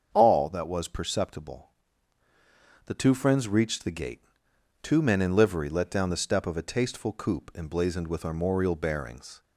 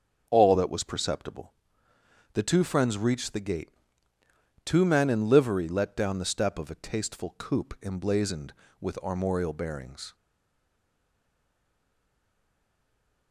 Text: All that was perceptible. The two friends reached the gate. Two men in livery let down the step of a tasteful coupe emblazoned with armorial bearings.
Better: first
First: starts louder than the rest; until 1.1 s; 7 dB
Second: starts louder than the rest; until 1.3 s; 7 dB // stays silent after the last word; strong; from 10.1 s on; 3.2 s long

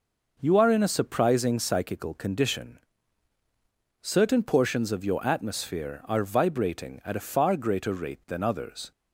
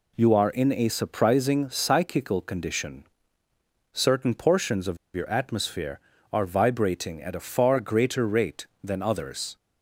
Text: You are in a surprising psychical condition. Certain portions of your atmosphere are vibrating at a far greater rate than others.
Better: first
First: none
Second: pauses between "of" and "your"; slight; at 4.9 s; 0.19 s long

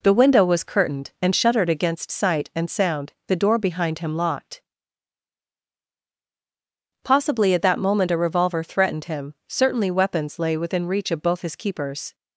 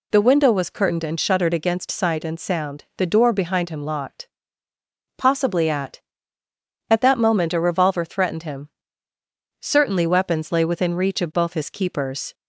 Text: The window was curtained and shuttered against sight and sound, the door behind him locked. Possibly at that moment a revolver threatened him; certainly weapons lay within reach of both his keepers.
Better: first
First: none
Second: says "at" twice; at 6.8 s

